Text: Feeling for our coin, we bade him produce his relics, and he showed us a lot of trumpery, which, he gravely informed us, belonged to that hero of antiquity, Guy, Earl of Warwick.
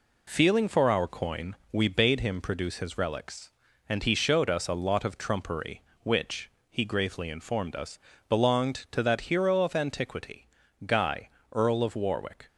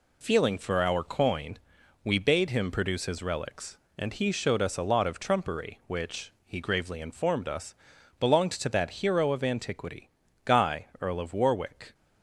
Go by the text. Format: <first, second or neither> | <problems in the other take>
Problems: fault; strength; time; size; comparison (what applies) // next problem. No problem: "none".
neither | none